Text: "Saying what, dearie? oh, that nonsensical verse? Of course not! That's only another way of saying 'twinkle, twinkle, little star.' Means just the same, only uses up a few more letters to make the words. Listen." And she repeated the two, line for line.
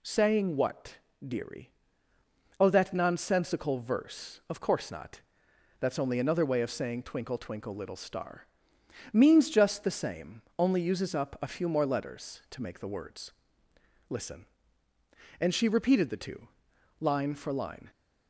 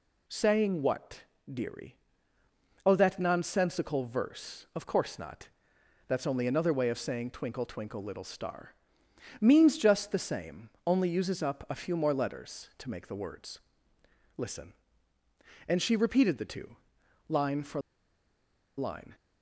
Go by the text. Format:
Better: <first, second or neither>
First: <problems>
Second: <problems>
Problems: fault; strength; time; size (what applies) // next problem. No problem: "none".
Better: first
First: none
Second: pauses between "for" and "line"; noticeable; at 17.8 s; 0.97 s long